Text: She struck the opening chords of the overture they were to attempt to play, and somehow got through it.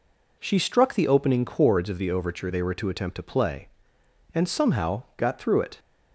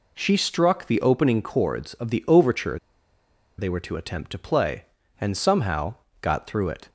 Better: first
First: none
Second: pauses between "overture" and "they"; noticeable; at 2.7 s; 0.80 s long // pauses between "somehow" and "got"; slight; at 5.9 s; 0.26 s long

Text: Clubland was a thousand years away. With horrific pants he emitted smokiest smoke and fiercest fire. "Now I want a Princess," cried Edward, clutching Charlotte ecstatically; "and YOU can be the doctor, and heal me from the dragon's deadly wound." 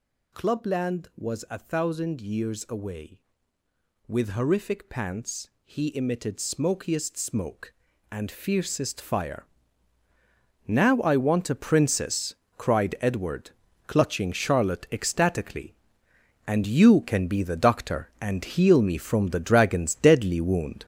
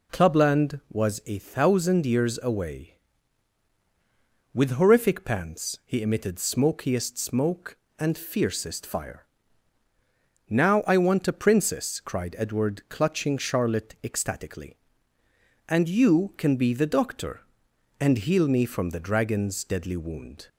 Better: second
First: gets louder; strong; throughout; 7.5 dB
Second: none

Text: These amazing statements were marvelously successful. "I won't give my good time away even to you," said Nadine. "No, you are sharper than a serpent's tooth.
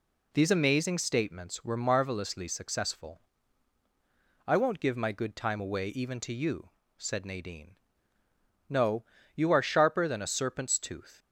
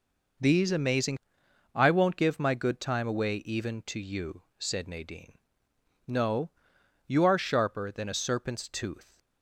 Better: first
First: none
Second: skips "statements were marvelously successful"; at 1.4 s

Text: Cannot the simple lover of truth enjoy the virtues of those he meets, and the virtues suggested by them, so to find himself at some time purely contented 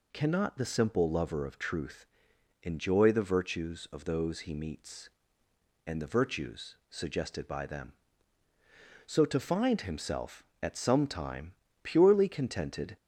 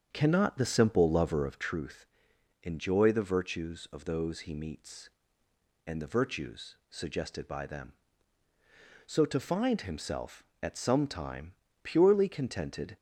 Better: first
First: pauses between "truth" and "enjoy"; noticeable; at 2.0 s; 0.56 s long // pauses between "time" and "purely"; slight; at 11.5 s; 0.32 s long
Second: starts louder than the rest; until 1.8 s; 7 dB // pauses between "truth" and "enjoy"; noticeable; at 2.0 s; 0.56 s long // pauses between "time" and "purely"; slight; at 11.5 s; 0.32 s long

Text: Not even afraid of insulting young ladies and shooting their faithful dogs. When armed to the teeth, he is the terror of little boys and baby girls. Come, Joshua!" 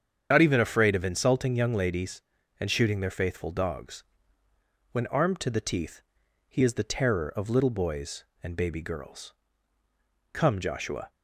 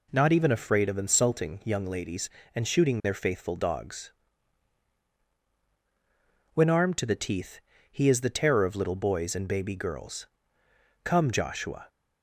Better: second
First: loses the start of "Not"; at 0.3 s; 50 ms // starts louder than the rest; strong; until 1.3 s; 8 dB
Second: none

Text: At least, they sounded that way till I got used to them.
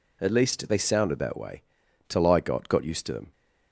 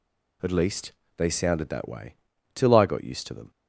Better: second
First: pauses between "way" and "till"; noticeable; at 1.6 s; 0.46 s long // says "got" twice; at 2.6 s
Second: pauses between "way" and "till"; at 2.1 s; 0.40 s long

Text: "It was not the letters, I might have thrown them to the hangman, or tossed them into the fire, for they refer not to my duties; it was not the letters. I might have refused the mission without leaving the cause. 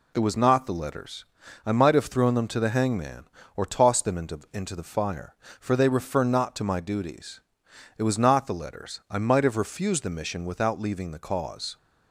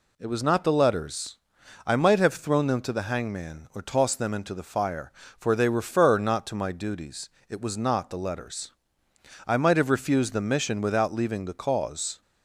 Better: second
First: says "into" twice; at 4.5 s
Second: none

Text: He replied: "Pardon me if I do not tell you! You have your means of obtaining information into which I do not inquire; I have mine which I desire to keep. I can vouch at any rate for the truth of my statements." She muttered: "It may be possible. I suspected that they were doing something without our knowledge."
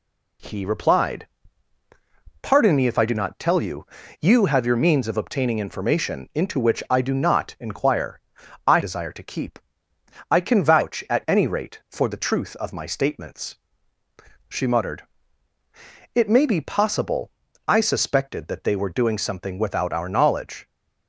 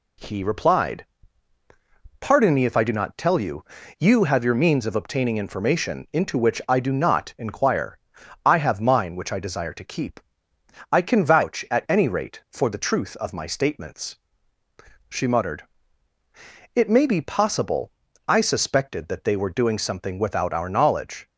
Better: second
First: skips "have mine which I"; at 8.7 s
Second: none

